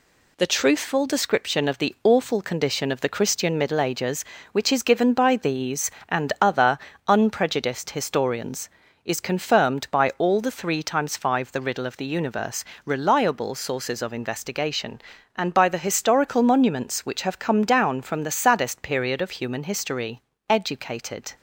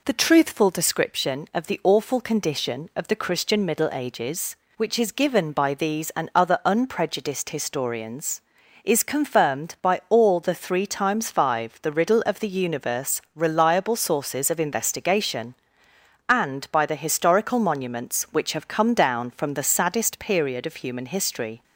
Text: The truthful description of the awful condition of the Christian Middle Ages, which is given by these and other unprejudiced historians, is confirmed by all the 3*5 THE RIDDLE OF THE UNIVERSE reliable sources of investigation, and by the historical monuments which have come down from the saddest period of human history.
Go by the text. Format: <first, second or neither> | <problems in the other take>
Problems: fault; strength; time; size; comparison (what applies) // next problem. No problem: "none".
second | pauses between "other" and "unprejudiced"; slight; at 6.7 s; 0.30 s long // pauses between "UNIVERSE" and "reliable"; slight; at 12.6 s; 0.20 s long // goes on to say "Educated"; noticeable; from 20.5 s on; 0.84 s long